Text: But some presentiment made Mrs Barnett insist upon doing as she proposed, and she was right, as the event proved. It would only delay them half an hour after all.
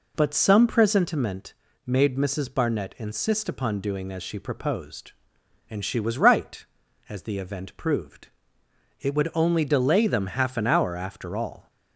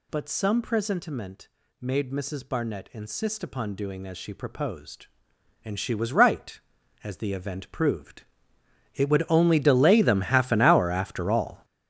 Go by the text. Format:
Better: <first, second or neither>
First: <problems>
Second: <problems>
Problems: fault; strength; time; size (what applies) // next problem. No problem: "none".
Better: first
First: pauses between "presentiment" and "made"; slight; at 1.5 s; 0.32 s long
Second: gets louder; strong; throughout; 10 dB // pauses between "presentiment" and "made"; slight; at 1.4 s; 0.32 s long